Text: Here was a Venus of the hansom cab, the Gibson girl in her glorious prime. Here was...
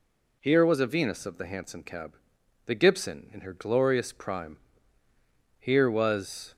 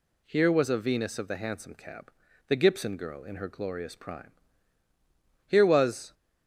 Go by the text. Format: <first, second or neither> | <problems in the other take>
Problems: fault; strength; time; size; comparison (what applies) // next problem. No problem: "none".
second | skips "girl"; at 3.3 s